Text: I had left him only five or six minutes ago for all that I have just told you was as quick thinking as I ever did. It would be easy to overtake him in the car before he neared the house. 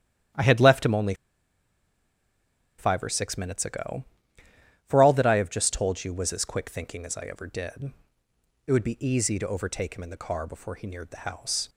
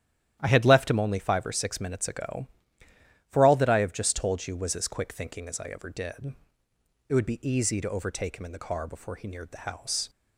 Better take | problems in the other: second | starts louder than the rest; strong; until 2.9 s; 11 dB; strong in the second // pauses between "only" and "five"; strong; at 1.1 s; 1.6 s long

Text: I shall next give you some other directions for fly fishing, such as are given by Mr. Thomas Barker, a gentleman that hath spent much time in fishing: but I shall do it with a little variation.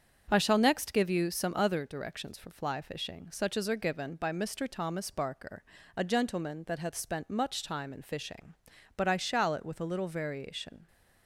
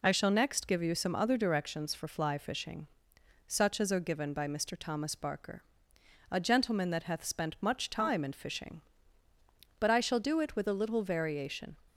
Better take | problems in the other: second | starts louder than the rest; until 1.3 s; 7 dB // skips "do"; at 9.5 s

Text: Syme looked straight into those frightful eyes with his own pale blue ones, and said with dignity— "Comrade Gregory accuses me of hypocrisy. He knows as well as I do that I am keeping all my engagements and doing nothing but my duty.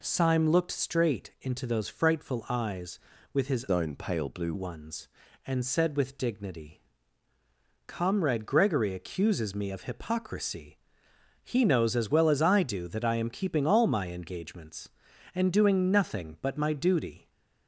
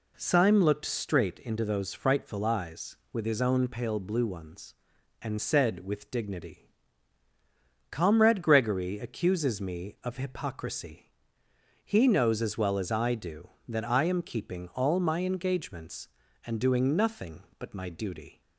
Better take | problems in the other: second | changes voice from "own" to "blue"; from 3.6 to 4.5 s; 0.9 s long

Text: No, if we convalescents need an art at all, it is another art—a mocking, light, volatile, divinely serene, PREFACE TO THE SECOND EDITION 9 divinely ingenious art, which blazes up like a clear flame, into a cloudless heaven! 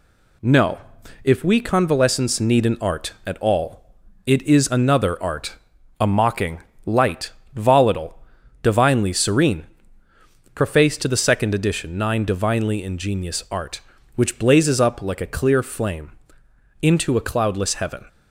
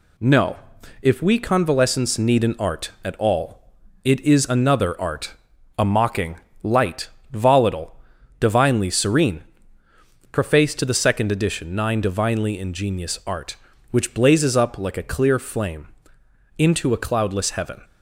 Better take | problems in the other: neither | none

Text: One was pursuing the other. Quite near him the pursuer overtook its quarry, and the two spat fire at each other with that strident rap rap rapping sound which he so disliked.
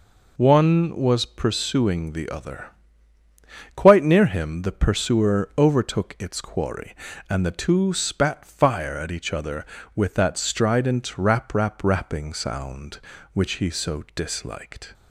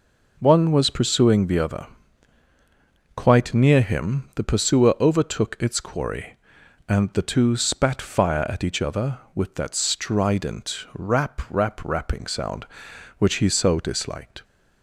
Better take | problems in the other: neither | none

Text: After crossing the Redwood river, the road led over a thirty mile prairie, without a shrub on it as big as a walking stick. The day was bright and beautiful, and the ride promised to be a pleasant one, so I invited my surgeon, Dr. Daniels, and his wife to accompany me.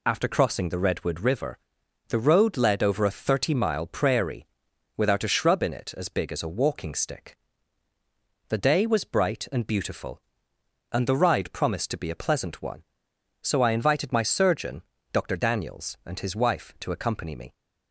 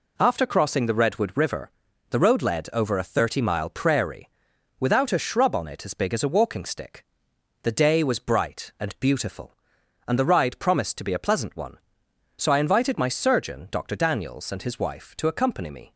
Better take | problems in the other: second | says "in" for "on"; at 5.6 s

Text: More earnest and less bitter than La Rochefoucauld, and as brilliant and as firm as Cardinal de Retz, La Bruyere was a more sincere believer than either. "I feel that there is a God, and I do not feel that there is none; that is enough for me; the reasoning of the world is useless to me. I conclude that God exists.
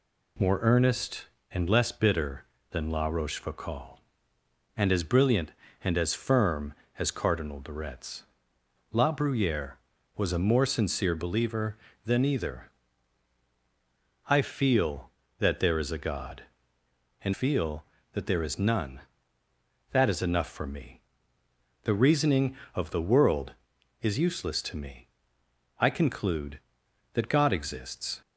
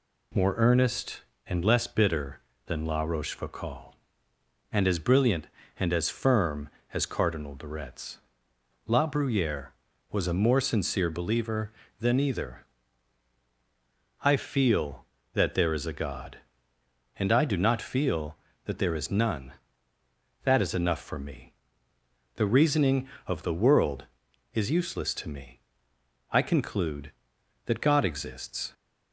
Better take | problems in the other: second | skips "I do not"; at 17.3 s

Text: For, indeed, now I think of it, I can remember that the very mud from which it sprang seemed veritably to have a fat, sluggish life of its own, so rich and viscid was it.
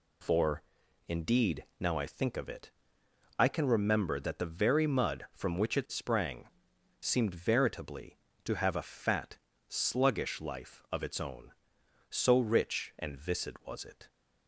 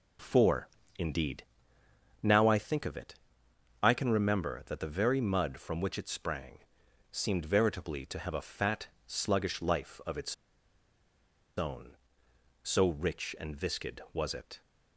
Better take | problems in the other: first | pauses between "sprang" and "seemed"; noticeable; at 6.5 s; 0.52 s long; noticeable in the first // pauses between "its" and "own"; at 10.3 s; 1.2 s long

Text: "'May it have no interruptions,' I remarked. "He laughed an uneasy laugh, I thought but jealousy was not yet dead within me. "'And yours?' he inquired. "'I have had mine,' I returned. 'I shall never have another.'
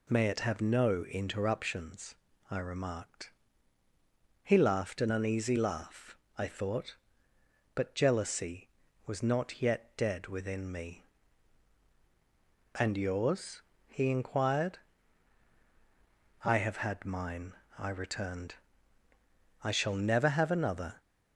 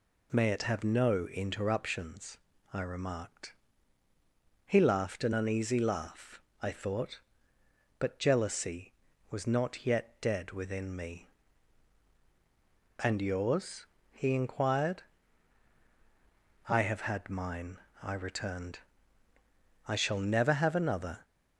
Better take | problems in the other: neither | none

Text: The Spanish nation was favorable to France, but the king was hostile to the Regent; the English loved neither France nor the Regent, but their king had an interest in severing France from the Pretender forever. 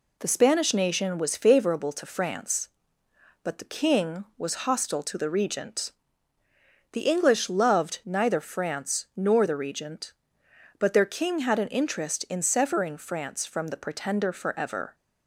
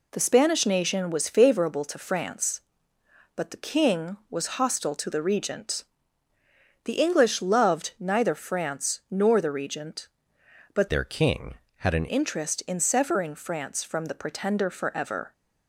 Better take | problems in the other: first | changes voice from "their" to "an"; from 10.8 to 12.0 s; 1.2 s long

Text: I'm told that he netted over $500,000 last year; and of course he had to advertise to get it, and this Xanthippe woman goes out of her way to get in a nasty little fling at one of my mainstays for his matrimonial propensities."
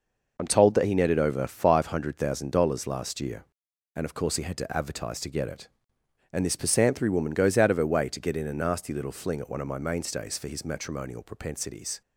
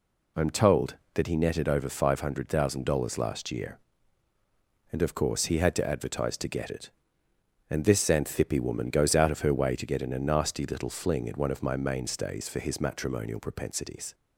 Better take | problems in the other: second | says "Pisanthry" for "Xanthippe"; at 6.5 s

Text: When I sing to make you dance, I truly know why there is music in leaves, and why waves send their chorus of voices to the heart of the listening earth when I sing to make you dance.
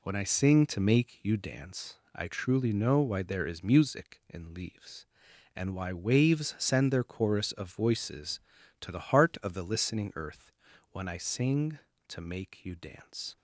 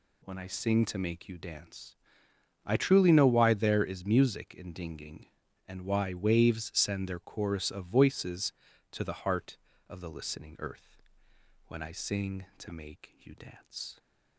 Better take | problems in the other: first | says "dinging" for "leaves"; at 4.7 s // pauses between "earth" and "when"; noticeable; at 11.0 s; 0.66 s long; also in the first

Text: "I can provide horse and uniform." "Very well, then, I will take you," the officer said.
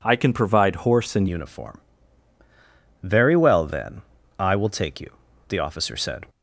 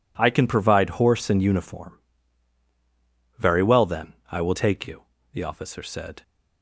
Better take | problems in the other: second | changes voice at "uniform"; from 1.2 s on; 5.0 s long

